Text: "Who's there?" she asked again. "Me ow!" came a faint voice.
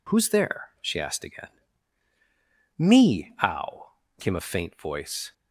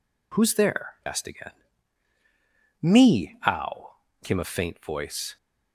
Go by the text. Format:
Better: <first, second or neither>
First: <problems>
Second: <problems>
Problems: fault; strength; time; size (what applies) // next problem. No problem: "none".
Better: first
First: none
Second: skips "she"; at 1.0 s